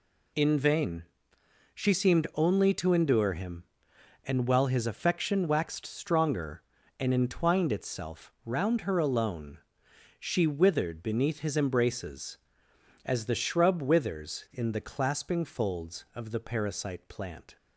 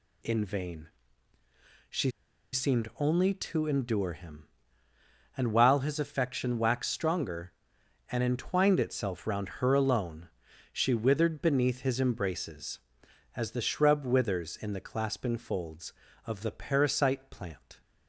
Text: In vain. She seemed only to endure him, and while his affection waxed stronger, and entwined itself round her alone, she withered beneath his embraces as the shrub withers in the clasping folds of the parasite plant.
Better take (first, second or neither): first